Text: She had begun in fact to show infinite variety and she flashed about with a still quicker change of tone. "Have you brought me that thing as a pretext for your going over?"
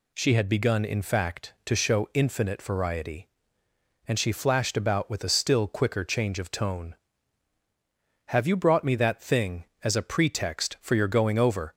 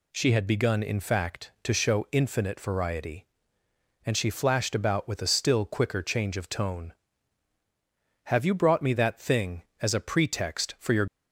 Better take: first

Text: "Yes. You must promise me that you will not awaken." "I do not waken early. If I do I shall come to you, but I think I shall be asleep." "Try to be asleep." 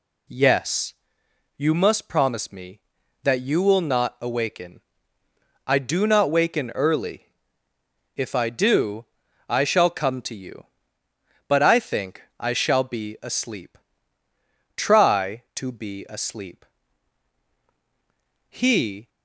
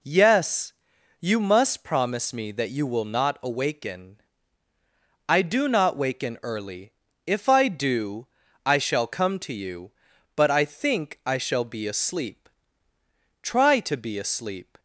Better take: second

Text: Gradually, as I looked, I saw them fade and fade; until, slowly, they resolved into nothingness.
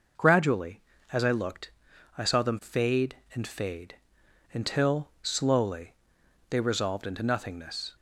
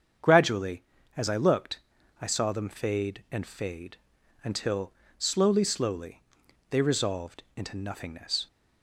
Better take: first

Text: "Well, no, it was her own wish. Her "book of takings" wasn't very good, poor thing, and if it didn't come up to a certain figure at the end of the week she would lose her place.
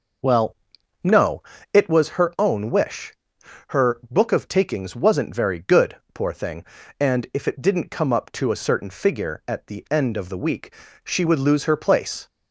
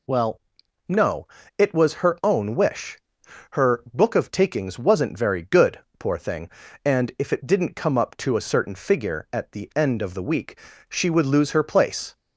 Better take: second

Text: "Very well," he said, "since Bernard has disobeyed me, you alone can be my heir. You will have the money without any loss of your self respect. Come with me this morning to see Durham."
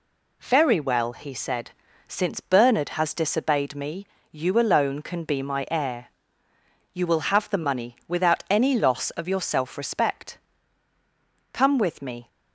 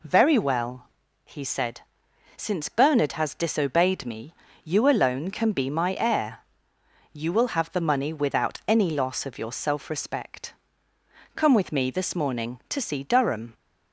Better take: second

